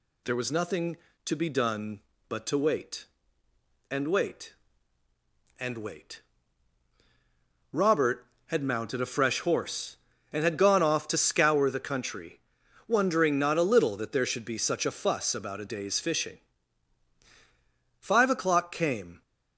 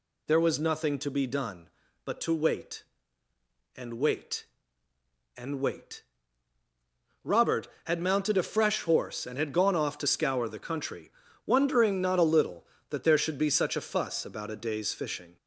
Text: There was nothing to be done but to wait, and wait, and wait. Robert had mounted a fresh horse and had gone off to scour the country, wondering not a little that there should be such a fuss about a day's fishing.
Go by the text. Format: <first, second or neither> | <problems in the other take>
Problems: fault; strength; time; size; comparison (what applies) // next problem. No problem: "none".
second | goes on to say "Five o'clock came"; noticeable; from 17.9 s on; 1.2 s long